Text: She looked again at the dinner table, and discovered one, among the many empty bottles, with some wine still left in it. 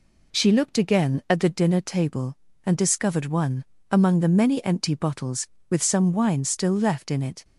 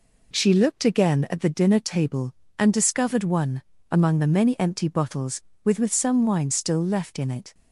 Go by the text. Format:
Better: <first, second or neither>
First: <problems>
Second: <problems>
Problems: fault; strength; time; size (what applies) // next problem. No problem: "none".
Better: first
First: none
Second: says "with" twice; at 5.7 s